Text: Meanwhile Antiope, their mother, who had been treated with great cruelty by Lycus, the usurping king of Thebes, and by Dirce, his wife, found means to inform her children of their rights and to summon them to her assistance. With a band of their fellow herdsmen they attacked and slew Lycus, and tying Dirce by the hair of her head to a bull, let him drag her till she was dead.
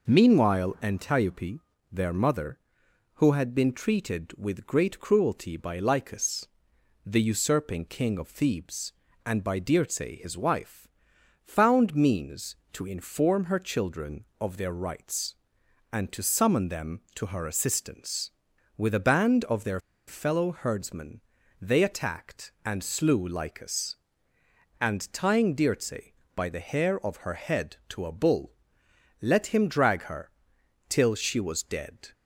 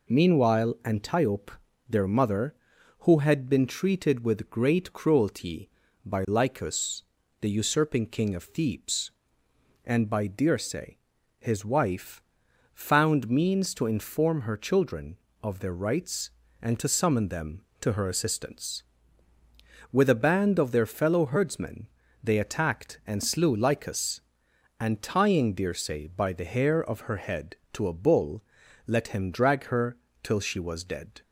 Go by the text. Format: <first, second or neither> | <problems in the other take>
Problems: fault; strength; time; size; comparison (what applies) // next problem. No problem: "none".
second | pauses between "their" and "fellow"; slight; at 19.7 s; 0.28 s long // pauses between "herdsmen" and "they"; at 21.1 s; 0.40 s long; slight in the second // pauses between "her" and "till"; noticeable; at 30.2 s; 0.58 s long; slight in the second